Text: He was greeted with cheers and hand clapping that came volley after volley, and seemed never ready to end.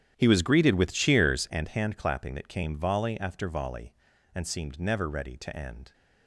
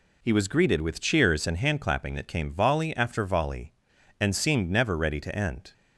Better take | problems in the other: second | starts louder than the rest; strong; until 1.6 s; 10 dB

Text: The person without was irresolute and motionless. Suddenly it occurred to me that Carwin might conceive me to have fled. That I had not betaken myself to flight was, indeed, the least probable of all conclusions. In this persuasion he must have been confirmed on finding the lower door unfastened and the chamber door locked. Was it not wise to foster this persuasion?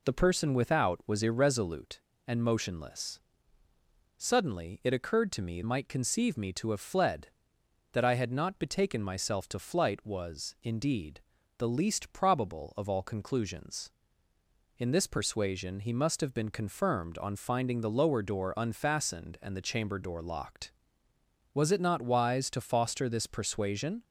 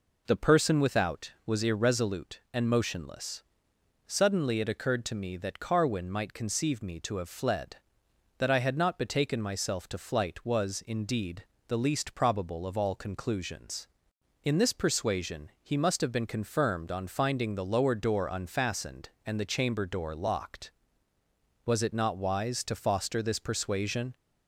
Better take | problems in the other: second | skips "that Carwin"; at 5.6 s

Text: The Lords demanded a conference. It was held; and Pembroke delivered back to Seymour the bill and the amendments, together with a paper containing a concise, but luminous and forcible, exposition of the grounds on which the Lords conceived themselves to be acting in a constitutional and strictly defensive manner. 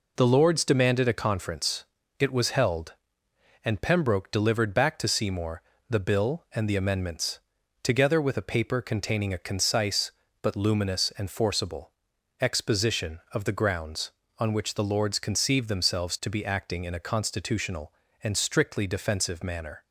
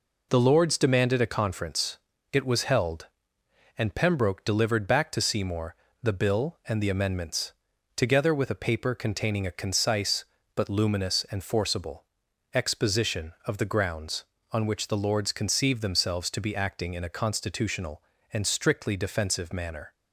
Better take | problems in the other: neither | pauses between "Seymour" and "the"; slight; the same in both

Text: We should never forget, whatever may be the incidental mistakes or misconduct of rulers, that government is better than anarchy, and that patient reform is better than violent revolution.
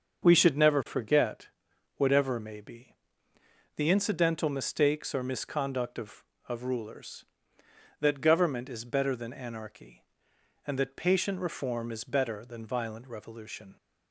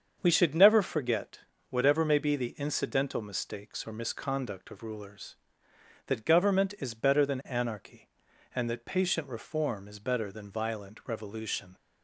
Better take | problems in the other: second | starts louder than the rest; until 1.2 s; 6.5 dB; also in the second // pauses between "be" and "the"; noticeable; at 2.9 s; 0.84 s long // says "of" twice; at 6.4 s

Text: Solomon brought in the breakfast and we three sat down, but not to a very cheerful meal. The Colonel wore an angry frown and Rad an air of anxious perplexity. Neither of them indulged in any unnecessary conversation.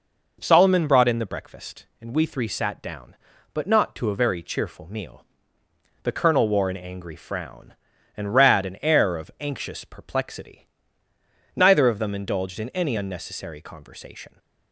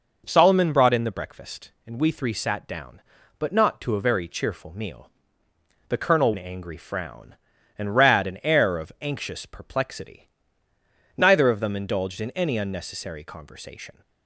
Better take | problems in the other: first | skips "wore"; at 6.3 s

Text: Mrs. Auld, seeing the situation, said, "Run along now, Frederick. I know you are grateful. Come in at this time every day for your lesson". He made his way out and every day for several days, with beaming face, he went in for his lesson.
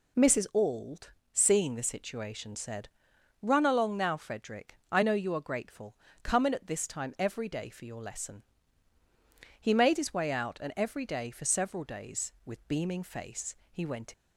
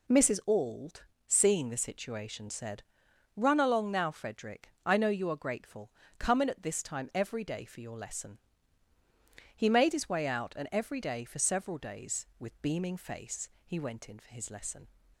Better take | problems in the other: second | stops before "in for his lesson"; at 14.1 s

